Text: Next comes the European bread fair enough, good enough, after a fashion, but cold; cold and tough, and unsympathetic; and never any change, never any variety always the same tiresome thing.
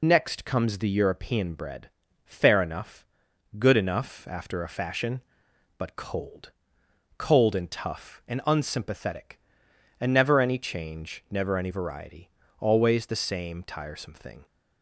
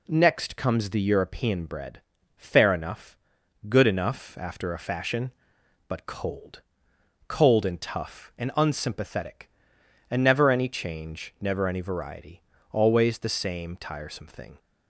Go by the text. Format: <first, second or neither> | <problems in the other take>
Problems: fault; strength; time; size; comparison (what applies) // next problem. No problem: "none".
second | loses the start of "Next"; at 0.0 s; 70 ms // pauses between "bread" and "fair"; slight; at 1.8 s; 0.36 s long; slight in the second // pauses between "variety" and "always"; slight; at 12.2 s; 0.28 s long; slight in the second